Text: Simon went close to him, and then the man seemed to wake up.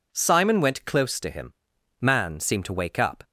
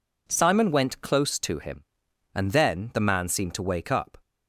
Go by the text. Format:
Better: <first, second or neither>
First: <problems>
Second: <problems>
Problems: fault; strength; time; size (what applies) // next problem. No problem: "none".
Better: second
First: skips "and then the"; at 1.7 s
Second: none